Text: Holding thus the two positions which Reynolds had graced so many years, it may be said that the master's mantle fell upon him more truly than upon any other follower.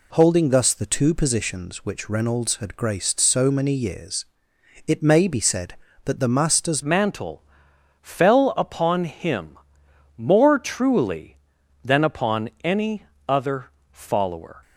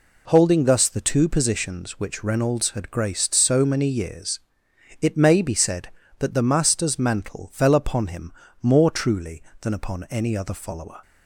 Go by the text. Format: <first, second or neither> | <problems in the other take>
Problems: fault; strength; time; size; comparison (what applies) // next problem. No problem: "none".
second | changes voice at "mantle"; from 6.8 s on; 7.7 s long // pauses between "mantle" and "fell"; noticeable; at 7.4 s; 0.60 s long // pauses between "him" and "more"; noticeable; at 9.5 s; 0.60 s long; slight in the second // pauses between "any" and "other"; slight; at 13.0 s; 0.22 s long // pauses between "other" and "follower"; slight; at 13.7 s; 0.20 s long